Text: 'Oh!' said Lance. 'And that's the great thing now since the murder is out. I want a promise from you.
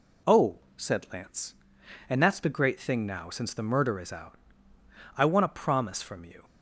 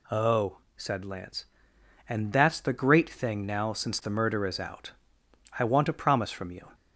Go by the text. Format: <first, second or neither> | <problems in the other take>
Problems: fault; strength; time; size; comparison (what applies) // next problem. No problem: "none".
neither | none